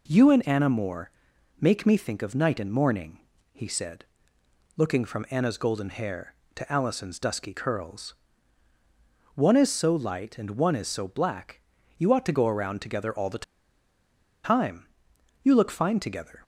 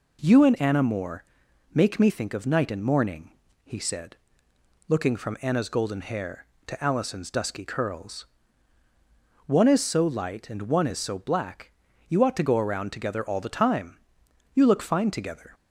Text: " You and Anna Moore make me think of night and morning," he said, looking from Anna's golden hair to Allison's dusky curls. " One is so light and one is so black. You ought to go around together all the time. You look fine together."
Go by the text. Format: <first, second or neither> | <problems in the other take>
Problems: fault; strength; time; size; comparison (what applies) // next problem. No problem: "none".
second | pauses between "Moore" and "make"; noticeable; at 1.1 s; 0.48 s long; noticeable in the second // pauses between "the" and "time"; at 13.4 s; 1.0 s long